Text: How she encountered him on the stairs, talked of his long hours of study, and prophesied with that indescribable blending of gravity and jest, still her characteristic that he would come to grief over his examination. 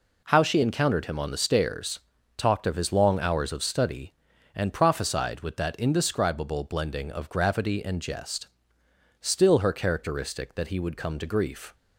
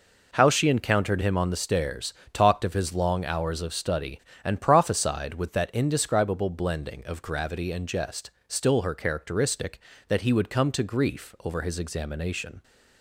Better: second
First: stops before "over his examination"; at 11.7 s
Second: none

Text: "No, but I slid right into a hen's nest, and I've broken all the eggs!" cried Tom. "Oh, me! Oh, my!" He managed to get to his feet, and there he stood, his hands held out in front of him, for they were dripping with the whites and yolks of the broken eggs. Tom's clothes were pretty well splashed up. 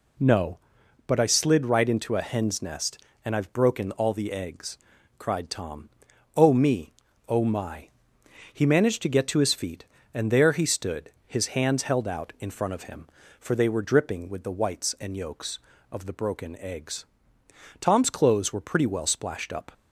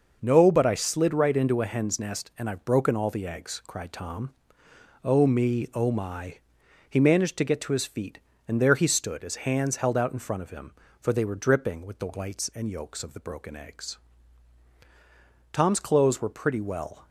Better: first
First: none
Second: stops before "splashed up"; at 17.0 s

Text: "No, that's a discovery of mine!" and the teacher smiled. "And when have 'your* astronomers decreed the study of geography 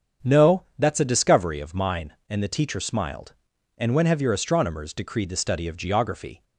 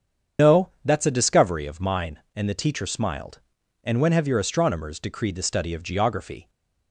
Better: first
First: starts louder than the rest; strong; until 1.3 s; 7.5 dB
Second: loses the start of "No"; at 0.3 s; 110 ms // starts louder than the rest; strong; until 1.5 s; 7.5 dB

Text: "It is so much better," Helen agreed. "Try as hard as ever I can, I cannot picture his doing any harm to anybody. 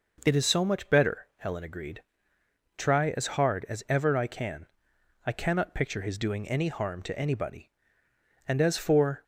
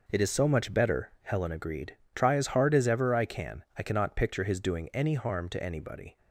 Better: second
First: goes on to say "And as for"; noticeable; from 8.4 s on; 0.78 s long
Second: none

